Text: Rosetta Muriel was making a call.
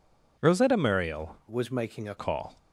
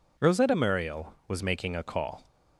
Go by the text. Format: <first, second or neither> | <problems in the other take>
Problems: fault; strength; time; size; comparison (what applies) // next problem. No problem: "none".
second | changes voice from "was" to "a"; from 1.4 to 2.1 s; 0.7 s long